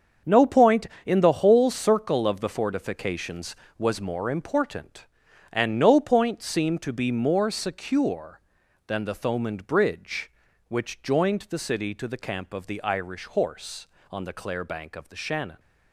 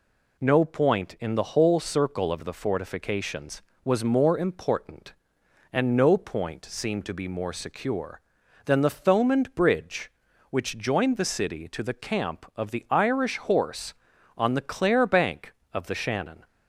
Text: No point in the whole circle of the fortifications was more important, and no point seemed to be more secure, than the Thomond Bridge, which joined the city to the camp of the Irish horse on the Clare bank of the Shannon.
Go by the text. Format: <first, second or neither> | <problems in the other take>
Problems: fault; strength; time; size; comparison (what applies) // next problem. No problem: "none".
second | gets quieter; strong; throughout; 10.5 dB